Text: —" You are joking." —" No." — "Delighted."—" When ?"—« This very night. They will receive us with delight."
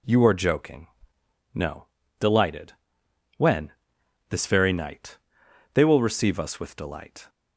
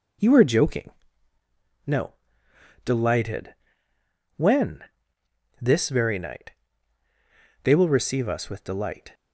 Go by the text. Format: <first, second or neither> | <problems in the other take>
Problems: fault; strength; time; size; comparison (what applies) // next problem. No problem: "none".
first | changes voice at "You"; from 0.1 s on; 9.0 s long